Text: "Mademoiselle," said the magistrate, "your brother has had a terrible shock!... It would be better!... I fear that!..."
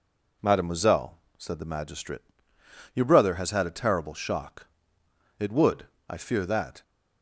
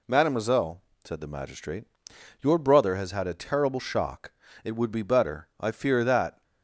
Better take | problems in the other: second | skips "be better"; at 5.9 s

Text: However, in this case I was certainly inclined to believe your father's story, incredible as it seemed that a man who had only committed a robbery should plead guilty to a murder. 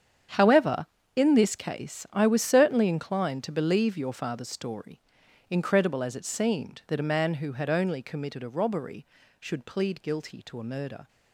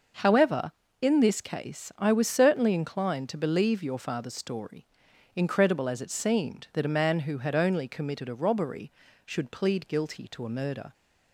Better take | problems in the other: second | gets quieter; strong; throughout; 14 dB // starts louder than the rest; strong; until 1.6 s; 8.5 dB; noticeable in the second

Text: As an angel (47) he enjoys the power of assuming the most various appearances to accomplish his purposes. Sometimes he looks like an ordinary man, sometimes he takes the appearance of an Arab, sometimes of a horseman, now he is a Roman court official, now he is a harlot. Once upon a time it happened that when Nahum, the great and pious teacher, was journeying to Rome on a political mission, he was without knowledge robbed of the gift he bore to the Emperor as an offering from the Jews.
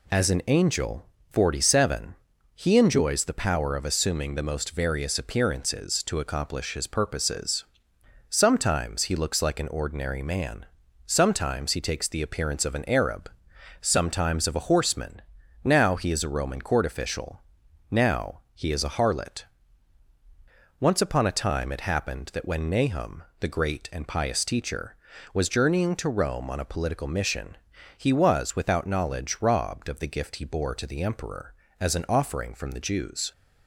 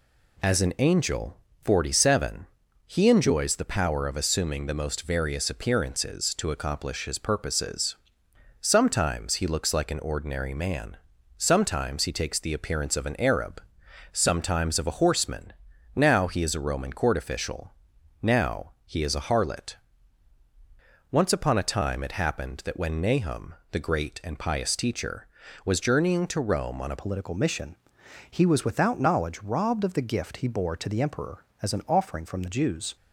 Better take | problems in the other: first | changes voice at "political"; from 26.9 s on; 6.0 s long

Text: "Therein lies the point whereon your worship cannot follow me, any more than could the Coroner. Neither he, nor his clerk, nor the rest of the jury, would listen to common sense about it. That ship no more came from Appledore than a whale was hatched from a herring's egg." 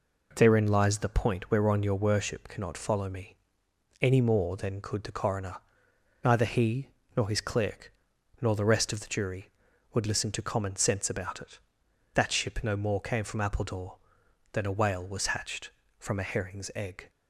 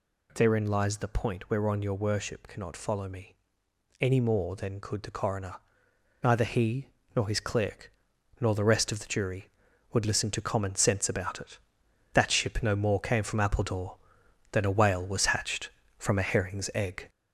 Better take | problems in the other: first | gets louder; noticeable; throughout; 4.5 dB

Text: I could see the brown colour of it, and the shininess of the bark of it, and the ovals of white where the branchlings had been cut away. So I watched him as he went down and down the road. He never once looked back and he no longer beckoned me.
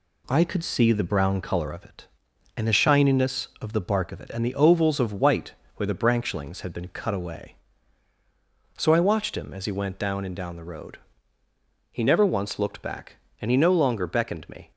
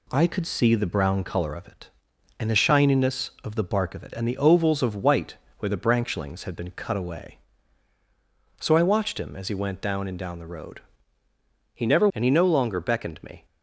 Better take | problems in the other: first | pauses between "white" and "where"; slight; at 5.3 s; 0.22 s long; slight in the first // skips "once looked back"; at 12.1 s

